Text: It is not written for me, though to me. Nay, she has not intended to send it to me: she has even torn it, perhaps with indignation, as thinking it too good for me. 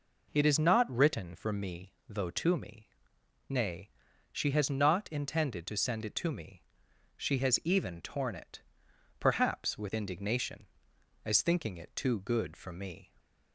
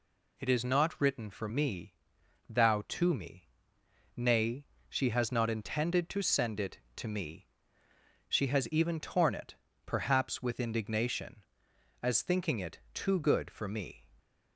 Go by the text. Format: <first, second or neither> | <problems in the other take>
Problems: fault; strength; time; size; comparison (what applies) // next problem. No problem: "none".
first | says "thou" for "though"; at 2.4 s